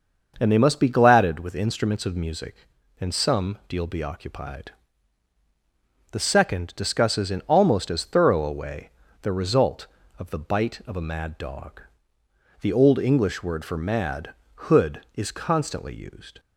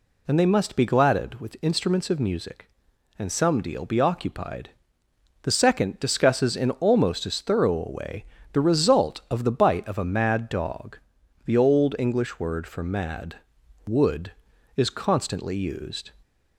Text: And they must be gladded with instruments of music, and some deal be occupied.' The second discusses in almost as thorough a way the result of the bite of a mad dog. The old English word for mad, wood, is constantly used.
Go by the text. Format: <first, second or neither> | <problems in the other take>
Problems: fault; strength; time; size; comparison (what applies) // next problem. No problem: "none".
second | starts louder than the rest; until 1.4 s; 6 dB // pauses between "way" and "the"; slight; at 8.8 s; 0.32 s long; slight in the second // says "hood" for "wood"; at 14.6 s